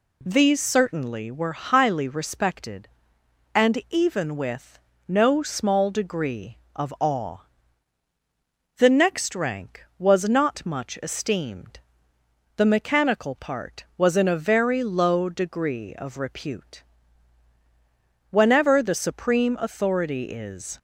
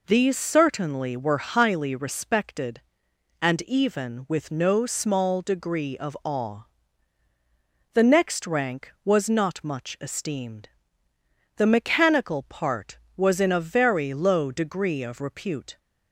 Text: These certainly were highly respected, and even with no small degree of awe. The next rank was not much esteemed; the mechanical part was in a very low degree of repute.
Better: second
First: pauses between "with" and "no"; slight; at 4.7 s; 0.30 s long // goes on to say "Whenever the supreme authority is"; strong; from 18.2 s on; 2.4 s long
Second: none

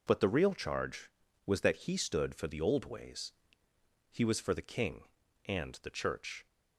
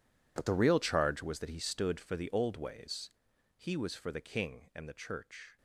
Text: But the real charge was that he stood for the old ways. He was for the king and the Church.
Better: first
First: none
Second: gets quieter; strong; throughout; 17 dB

